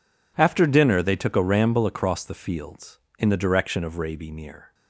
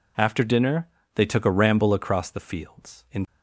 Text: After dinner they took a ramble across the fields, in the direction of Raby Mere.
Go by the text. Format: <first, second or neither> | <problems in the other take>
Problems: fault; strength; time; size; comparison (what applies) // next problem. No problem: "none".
first | pauses between "dinner" and "they"; slight; at 0.8 s; 0.26 s long // stops before "the direction of Raby Mere"; at 3.2 s